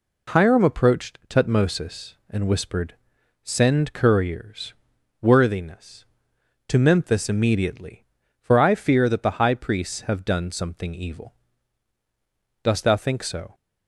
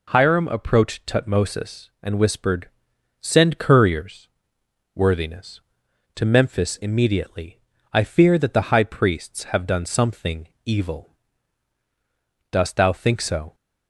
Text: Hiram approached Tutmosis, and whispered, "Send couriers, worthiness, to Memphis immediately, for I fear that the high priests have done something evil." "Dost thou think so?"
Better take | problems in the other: first | skips "for"; at 7.7 s // pauses between "something" and "evil"; slight; at 10.4 s; 0.16 s long

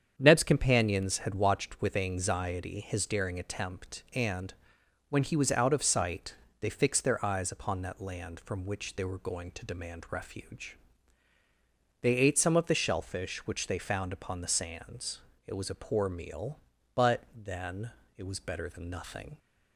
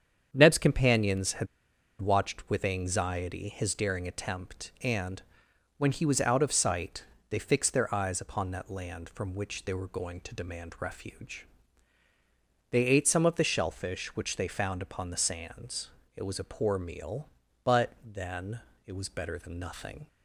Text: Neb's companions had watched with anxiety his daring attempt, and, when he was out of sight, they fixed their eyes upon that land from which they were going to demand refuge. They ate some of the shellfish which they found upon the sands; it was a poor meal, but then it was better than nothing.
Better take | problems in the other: first | starts louder than the rest; strong; until 1.3 s; 8 dB; strong in the first // pauses between "had" and "watched"; noticeable; at 1.4 s; 0.54 s long // pauses between "then" and "it"; slight; at 18.5 s; 0.26 s long; slight in the first

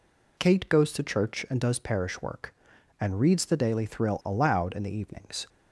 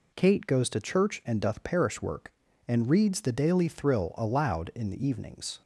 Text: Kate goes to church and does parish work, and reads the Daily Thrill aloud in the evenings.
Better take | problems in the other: first | says "doth" for "does"; at 1.4 s

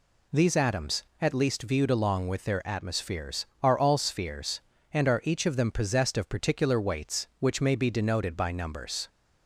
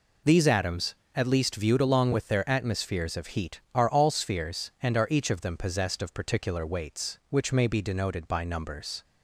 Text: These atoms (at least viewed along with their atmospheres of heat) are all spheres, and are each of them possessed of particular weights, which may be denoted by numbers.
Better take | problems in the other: second | skips "of heat"; at 3.5 s

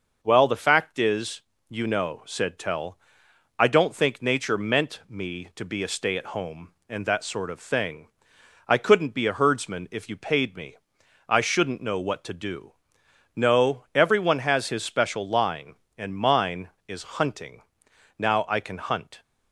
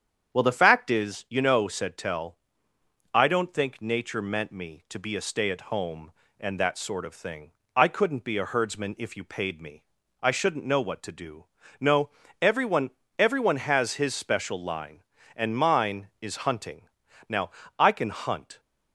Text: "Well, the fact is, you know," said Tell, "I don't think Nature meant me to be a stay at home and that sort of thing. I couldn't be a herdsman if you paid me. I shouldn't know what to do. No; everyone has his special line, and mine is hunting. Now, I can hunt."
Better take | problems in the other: first | starts louder than the rest; strong; until 1.4 s; 8 dB; noticeable in the first // says "everyone" twice; at 13.1 s

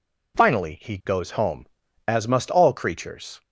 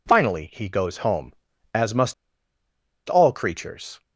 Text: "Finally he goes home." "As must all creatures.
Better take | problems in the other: first | pauses between "must" and "all"; noticeable; at 2.1 s; 0.95 s long

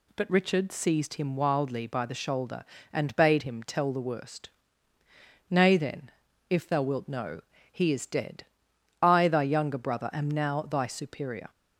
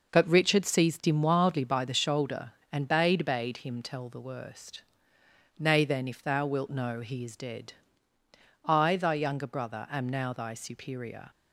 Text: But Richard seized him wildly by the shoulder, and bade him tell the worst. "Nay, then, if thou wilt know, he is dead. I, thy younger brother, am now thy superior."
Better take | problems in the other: first | says "bade" twice; at 3.2 s

